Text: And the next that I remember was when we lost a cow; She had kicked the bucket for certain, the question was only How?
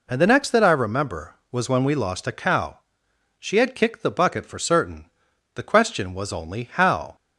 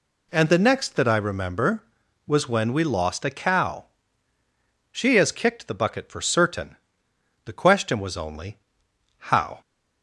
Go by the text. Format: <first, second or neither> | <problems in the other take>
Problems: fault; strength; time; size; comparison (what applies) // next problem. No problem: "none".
first | says "has" for "had"; at 5.1 s // pauses between "only" and "How"; noticeable; at 8.5 s; 0.58 s long